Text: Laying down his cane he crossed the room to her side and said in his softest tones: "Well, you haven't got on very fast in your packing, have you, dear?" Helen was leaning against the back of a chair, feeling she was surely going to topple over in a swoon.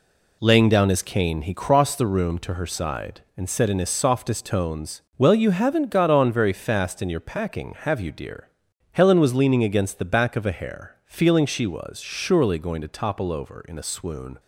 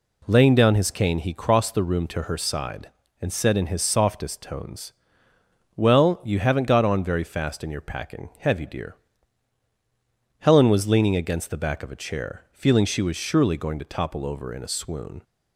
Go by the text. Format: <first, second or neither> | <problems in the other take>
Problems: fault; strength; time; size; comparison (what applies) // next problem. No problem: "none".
second | says "hair" for "chair"; at 10.5 s